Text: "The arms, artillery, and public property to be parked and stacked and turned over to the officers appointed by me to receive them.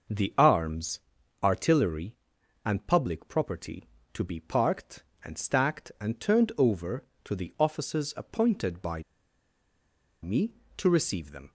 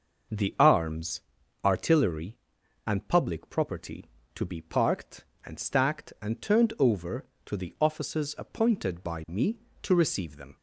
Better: second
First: starts louder than the rest; noticeable; until 1.5 s; 6 dB // pauses between "by" and "me"; at 9.0 s; 1.2 s long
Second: starts louder than the rest; noticeable; until 1.7 s; 6 dB

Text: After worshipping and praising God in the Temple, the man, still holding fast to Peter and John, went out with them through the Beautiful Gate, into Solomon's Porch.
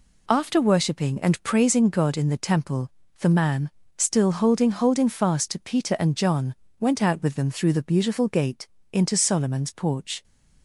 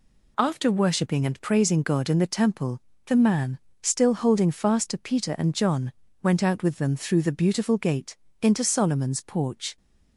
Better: second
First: says "holding" twice; at 4.7 s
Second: none

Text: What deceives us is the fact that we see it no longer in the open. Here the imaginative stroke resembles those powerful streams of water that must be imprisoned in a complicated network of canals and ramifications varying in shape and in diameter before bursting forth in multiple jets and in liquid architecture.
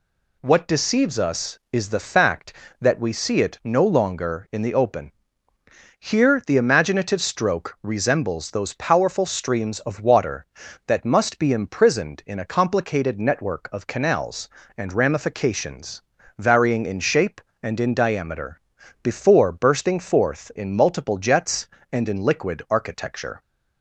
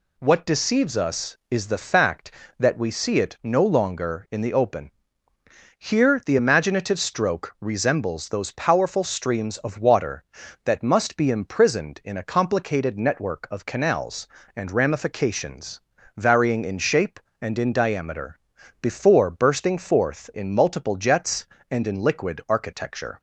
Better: neither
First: pauses between "ramifications" and "varying"; slight; at 16.0 s; 0.34 s long // pauses between "diameter" and "before"; at 18.6 s; 0.40 s long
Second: pauses between "ramifications" and "varying"; slight; at 15.8 s; 0.34 s long // pauses between "diameter" and "before"; at 18.3 s; 0.40 s long

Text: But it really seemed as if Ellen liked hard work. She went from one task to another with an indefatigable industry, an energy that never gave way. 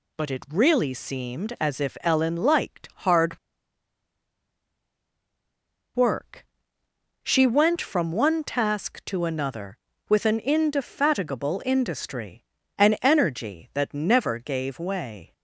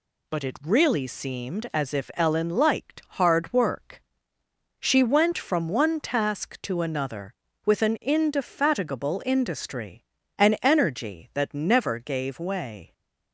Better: second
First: pauses between "hard" and "work"; strong; at 3.3 s; 2.5 s long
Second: none

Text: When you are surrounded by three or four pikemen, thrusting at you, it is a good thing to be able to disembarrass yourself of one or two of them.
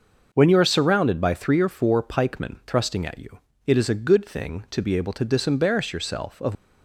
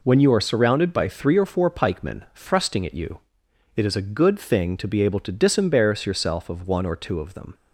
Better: second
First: stops before "one or two of them"; at 6.5 s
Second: none

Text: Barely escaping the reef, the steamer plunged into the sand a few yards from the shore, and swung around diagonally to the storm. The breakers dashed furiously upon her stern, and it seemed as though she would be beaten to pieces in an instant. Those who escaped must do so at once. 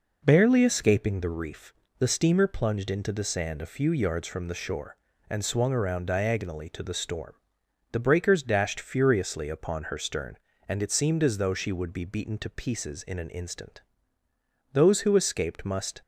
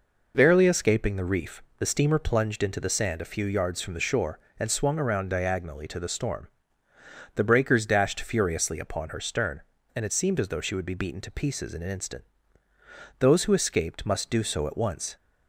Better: second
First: stops before "do so at once"; at 16.0 s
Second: none

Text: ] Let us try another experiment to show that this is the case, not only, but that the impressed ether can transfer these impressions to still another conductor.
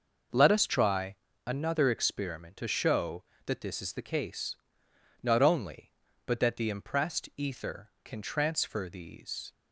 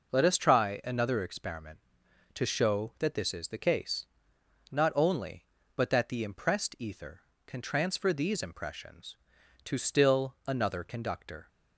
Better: second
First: pauses between "try" and "another"; slight; at 1.1 s; 0.28 s long // stops before "impressions to still another conductor"; at 9.5 s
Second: none

